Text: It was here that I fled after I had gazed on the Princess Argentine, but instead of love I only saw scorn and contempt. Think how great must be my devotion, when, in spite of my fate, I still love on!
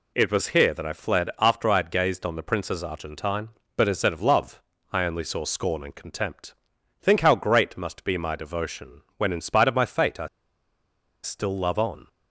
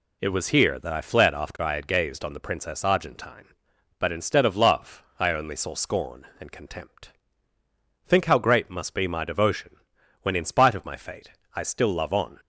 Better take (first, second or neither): second